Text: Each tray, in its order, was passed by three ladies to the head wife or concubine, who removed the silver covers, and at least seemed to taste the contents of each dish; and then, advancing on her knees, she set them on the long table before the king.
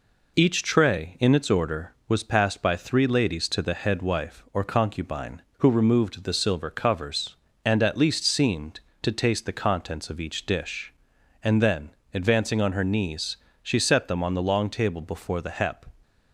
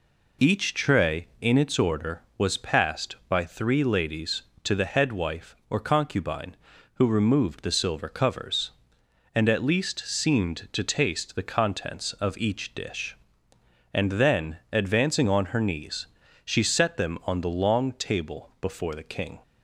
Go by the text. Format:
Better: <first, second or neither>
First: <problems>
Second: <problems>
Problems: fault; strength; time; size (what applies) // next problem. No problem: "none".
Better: second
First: says "hep" for "king"; at 15.5 s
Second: none